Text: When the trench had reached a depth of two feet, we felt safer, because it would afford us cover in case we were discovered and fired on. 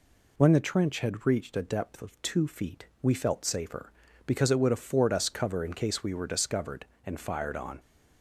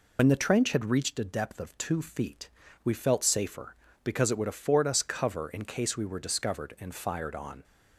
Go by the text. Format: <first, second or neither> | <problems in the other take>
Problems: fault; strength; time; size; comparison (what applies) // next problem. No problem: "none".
first | loses the start of "When"; at 0.1 s; 60 ms